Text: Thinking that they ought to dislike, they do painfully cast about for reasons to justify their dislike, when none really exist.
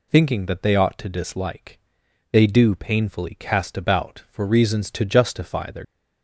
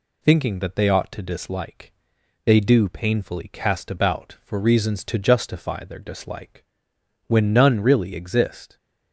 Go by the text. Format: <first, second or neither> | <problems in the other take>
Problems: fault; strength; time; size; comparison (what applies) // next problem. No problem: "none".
second | stops before "dislike when none really exist"; at 5.8 s